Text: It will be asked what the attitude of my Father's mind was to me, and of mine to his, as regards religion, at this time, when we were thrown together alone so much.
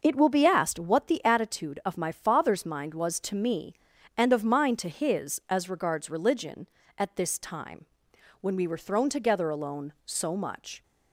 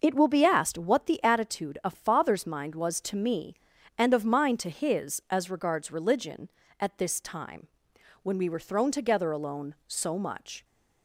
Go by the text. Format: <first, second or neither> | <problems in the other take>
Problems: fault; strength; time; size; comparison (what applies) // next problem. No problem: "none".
first | skips "my"; at 1.9 s